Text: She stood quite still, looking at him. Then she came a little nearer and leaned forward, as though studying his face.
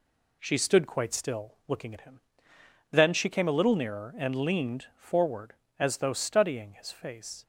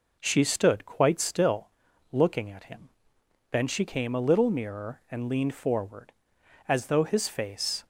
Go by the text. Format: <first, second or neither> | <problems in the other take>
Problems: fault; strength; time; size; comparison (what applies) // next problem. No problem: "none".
first | skips "studying"; at 7.0 s